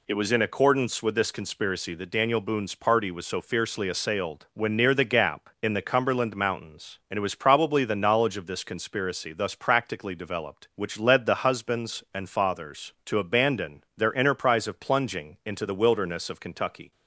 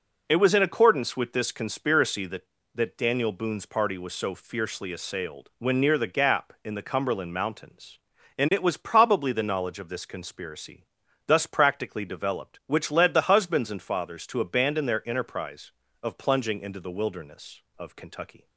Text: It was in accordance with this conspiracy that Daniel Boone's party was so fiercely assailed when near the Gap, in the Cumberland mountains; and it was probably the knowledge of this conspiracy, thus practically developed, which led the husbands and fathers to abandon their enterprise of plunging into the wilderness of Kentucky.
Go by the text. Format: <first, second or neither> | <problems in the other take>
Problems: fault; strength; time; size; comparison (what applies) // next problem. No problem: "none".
first | says "that" twice; at 2.7 s